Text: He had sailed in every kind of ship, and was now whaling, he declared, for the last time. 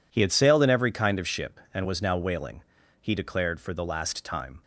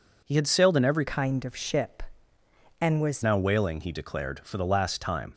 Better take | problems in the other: first | changes voice from "kind" to "was"; from 1.0 to 3.2 s; 2.2 s long

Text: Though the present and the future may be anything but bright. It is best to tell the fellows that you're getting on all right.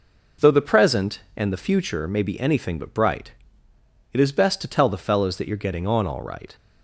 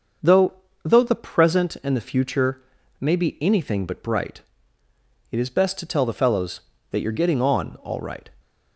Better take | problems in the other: first | starts louder than the rest; until 1.5 s; 6 dB // says "Though" twice; at 0.8 s // pauses between "future" and "may"; at 2.6 s; 0.38 s long

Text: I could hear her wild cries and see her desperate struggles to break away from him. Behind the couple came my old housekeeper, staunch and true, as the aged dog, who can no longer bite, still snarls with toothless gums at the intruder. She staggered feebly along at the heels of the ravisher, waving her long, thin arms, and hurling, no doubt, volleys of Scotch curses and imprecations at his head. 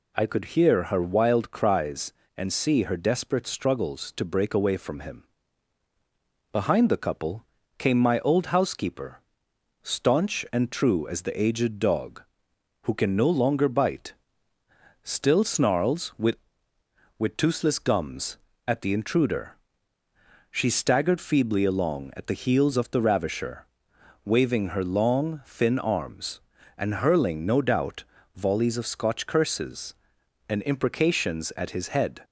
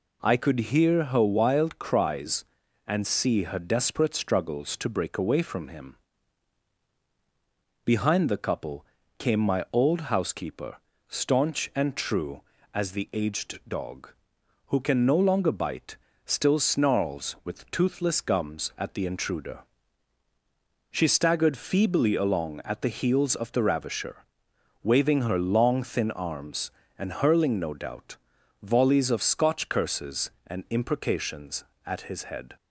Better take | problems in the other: second | pauses between "couple" and "came"; slight; at 7.4 s; 0.34 s long; slight in the second // says "with" twice; at 17.1 s

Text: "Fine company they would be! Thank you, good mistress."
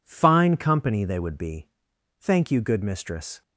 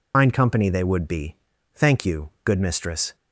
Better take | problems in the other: first | loses the start of "Fine"; at 0.1 s; 100 ms

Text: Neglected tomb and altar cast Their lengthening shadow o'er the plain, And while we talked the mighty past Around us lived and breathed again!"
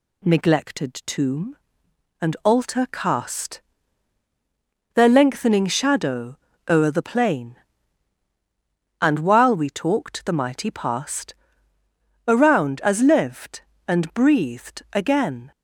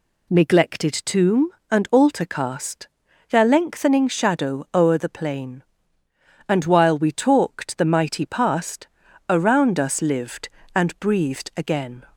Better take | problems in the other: second | pauses between "cast" and "Their"; strong; at 3.6 s; 1.3 s long; also in the second // pauses between "shadow" and "o'er"; slight; at 6.3 s; 0.32 s long // pauses between "past" and "Around"; noticeable; at 11.3 s; 0.90 s long; also in the second // says "as" for "us"; at 12.8 s

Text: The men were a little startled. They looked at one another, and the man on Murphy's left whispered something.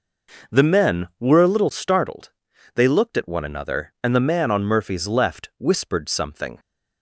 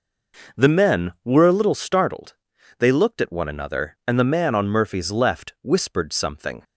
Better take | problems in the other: neither | none

